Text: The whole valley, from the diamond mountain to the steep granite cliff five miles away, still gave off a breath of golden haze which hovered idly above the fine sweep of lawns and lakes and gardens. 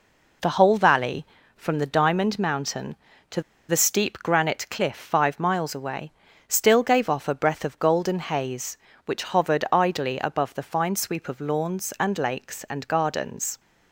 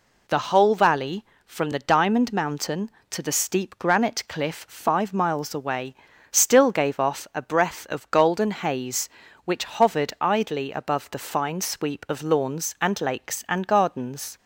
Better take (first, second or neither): second